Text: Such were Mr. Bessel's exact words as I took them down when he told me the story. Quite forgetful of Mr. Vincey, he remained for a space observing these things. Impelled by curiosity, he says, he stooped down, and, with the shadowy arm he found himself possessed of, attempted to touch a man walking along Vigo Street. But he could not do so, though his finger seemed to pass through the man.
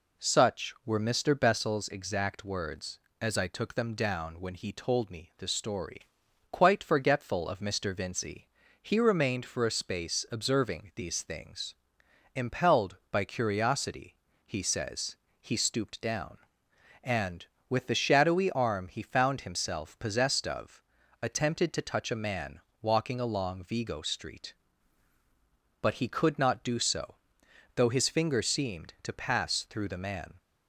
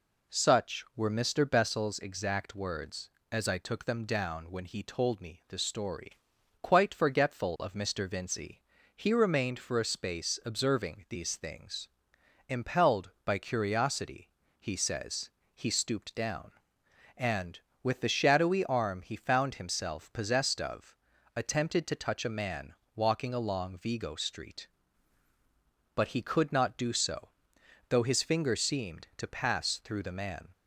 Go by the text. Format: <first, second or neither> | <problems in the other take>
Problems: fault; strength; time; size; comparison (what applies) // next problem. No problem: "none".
neither | pauses between "man" and "walking"; slight; the same in both